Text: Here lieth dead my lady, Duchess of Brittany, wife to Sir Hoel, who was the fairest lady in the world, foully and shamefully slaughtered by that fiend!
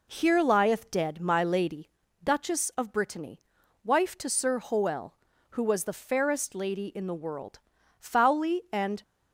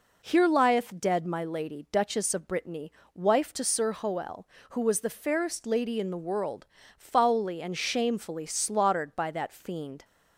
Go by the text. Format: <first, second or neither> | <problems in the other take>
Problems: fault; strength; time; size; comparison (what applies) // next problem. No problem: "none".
second | stops before "shamefully slaughtered by that fiend"; at 9.0 s